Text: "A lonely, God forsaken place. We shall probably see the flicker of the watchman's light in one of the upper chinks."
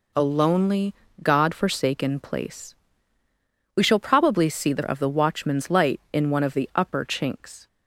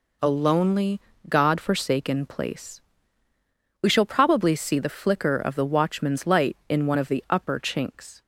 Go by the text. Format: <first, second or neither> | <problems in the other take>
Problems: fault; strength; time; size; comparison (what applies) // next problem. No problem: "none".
second | skips "flicker"; at 4.8 s